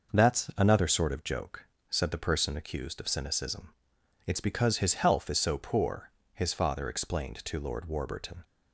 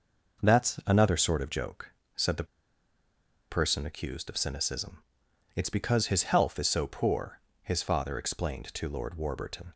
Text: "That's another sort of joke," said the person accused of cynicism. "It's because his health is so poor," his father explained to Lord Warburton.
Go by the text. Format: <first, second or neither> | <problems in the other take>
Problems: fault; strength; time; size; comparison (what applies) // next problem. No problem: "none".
first | pauses between "the" and "person"; at 2.4 s; 1.0 s long